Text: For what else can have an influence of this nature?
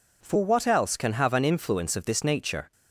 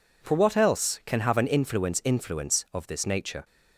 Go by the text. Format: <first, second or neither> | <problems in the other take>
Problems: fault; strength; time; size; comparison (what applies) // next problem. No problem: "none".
first | says "influence" twice; at 2.0 s